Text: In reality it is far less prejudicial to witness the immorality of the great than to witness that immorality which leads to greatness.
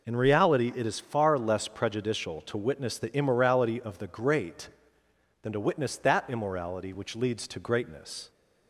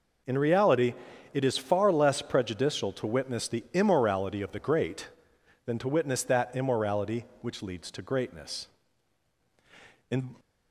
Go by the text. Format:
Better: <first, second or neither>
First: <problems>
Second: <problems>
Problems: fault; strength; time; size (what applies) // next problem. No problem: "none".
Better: first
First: none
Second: pauses between "reality" and "it"; at 0.9 s; 0.38 s long // goes on to say "In"; slight; from 10.1 s on; 0.24 s long